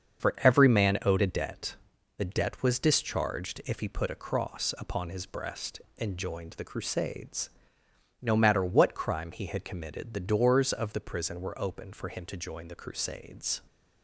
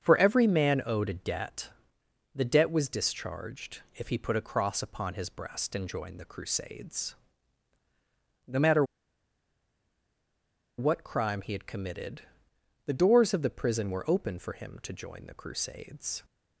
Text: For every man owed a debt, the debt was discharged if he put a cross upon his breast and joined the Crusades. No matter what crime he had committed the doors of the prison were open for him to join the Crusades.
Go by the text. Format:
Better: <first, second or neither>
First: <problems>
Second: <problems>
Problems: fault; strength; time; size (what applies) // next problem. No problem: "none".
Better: first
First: starts louder than the rest; until 1.2 s; 7 dB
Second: starts louder than the rest; strong; until 1.0 s; 7.5 dB // pauses between "matter" and "what"; strong; at 8.8 s; 1.9 s long // pauses between "committed" and "the"; noticeable; at 12.2 s; 0.62 s long